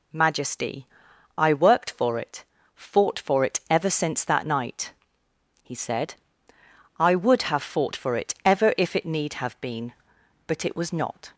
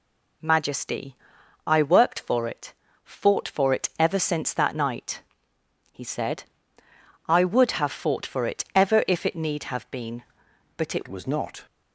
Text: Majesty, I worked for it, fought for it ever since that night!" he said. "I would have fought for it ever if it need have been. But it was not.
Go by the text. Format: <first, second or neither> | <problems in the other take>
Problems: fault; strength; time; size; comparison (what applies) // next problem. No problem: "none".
first | changes voice at "was"; from 11.0 s on; 0.6 s long